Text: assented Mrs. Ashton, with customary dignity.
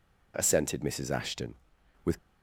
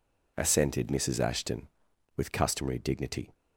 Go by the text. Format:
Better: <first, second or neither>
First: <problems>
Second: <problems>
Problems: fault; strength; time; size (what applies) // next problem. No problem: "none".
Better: second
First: stops before "customary dignity"; at 2.1 s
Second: none